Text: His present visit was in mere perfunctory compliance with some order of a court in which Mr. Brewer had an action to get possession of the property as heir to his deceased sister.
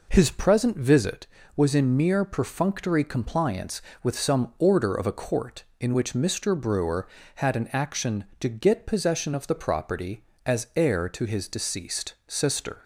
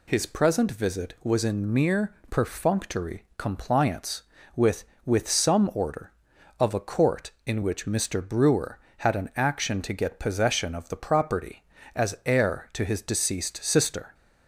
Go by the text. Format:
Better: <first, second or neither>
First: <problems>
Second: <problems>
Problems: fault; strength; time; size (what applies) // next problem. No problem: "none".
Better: first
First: none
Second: pauses between "mere" and "perfunctory"; slight; at 2.1 s; 0.16 s long // says "with" twice; at 5.0 s